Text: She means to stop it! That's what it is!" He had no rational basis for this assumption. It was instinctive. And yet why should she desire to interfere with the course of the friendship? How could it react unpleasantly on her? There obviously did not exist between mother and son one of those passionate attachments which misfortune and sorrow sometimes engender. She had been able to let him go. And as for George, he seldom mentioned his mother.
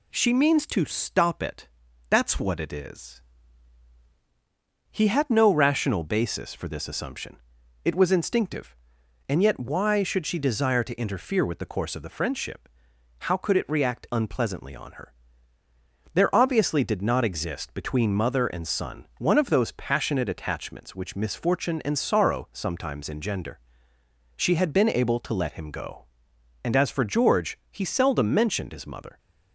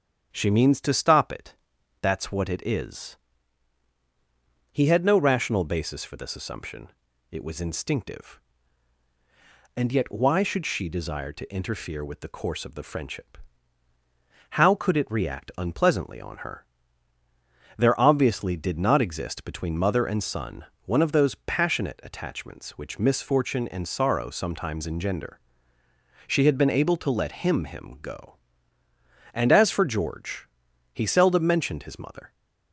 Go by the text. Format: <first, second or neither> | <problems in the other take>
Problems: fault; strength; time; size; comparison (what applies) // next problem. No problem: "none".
first | starts louder than the rest; strong; until 1.3 s; 8.5 dB // pauses between "son" and "one"; slight; at 20.6 s; 0.20 s long // says "him" twice; at 27.6 s